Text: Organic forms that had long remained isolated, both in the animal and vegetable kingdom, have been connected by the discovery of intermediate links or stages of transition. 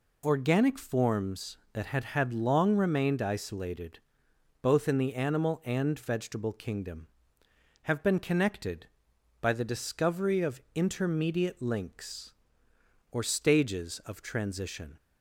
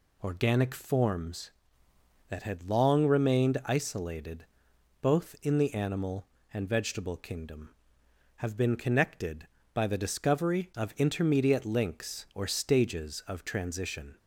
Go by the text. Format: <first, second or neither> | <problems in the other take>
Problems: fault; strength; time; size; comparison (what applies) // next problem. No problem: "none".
second | says "had" twice; at 2.0 s